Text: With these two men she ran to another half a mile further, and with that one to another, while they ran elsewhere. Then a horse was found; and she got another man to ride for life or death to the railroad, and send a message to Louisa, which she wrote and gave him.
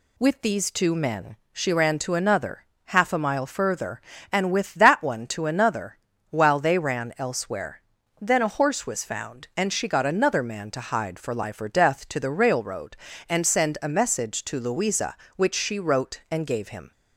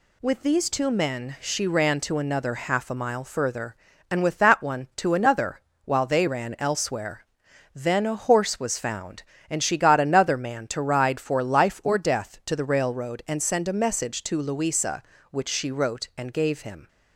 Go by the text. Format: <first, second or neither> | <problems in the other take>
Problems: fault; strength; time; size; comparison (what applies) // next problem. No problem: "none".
second | pauses between "men" and "she"; slight; at 1.3 s; 0.16 s long // pauses between "another" and "half"; slight; at 2.6 s; 0.20 s long // says "hide" for "ride"; at 10.8 s